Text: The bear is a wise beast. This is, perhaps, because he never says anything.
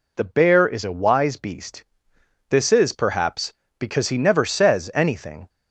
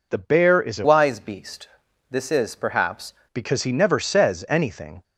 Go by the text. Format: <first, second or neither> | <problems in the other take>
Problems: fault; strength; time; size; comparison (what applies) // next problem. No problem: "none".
first | changes voice from "wise" to "perhaps"; from 0.8 to 3.1 s; 2.3 s long